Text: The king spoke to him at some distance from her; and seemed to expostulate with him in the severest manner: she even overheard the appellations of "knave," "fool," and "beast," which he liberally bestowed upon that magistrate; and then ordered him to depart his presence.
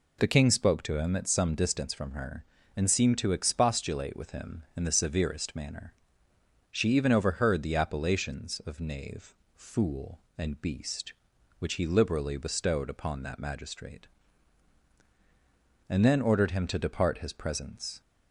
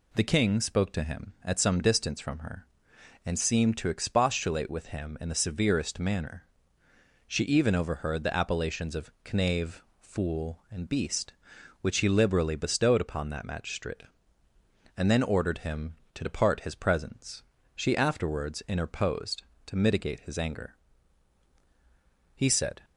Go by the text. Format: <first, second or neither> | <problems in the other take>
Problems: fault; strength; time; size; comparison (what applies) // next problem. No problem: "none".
first | pauses between "of" and "knave"; slight; at 9.1 s; 0.22 s long // goes on to say "She afterwards interposed to mitigate his anger he said"; strong; from 17.7 s on; 5.0 s long